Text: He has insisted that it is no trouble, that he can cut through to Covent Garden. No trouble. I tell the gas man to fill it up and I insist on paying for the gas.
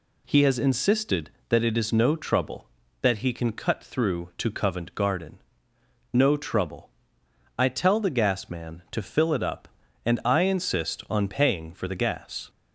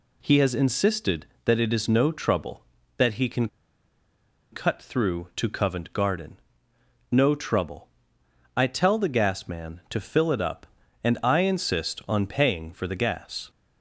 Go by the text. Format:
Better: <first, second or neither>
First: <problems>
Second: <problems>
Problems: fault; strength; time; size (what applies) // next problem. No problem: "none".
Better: first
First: none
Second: pauses between "can" and "cut"; at 3.4 s; 1.0 s long